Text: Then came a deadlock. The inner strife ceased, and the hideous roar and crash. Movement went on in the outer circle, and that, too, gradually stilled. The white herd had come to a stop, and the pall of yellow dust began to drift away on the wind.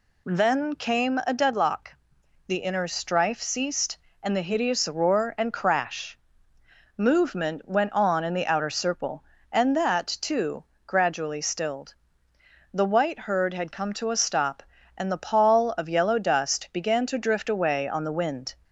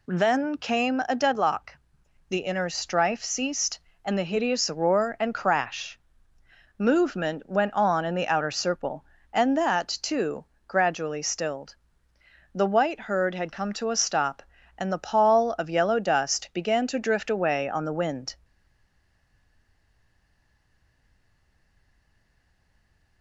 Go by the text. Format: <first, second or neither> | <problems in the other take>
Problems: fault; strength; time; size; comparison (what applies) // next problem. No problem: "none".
first | stays silent after the last word; strong; from 18.4 s on; 4.8 s long